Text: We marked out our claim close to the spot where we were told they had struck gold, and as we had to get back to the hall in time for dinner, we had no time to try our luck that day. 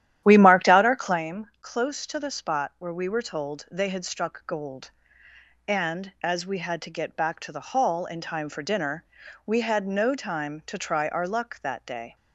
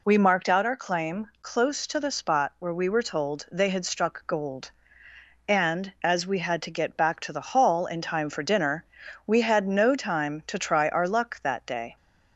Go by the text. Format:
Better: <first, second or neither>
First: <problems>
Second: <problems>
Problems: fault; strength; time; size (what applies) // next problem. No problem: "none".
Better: second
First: starts louder than the rest; strong; until 1.2 s; 11.5 dB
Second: none